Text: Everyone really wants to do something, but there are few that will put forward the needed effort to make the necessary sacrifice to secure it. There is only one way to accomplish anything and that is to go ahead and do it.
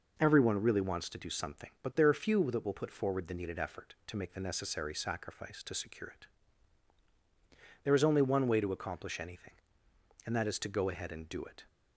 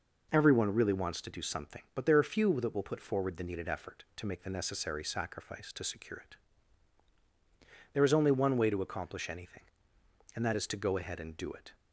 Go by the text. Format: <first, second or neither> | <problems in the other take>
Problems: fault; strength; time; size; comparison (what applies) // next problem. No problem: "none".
neither | none